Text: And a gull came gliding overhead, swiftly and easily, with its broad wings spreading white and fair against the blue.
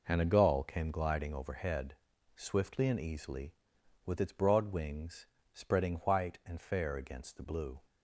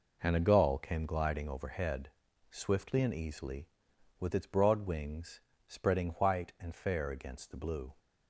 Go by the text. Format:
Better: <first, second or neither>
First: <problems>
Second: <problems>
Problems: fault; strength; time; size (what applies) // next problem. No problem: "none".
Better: neither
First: pauses between "wings" and "spreading"; slight; at 5.2 s; 0.28 s long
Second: pauses between "wings" and "spreading"; slight; at 5.3 s; 0.28 s long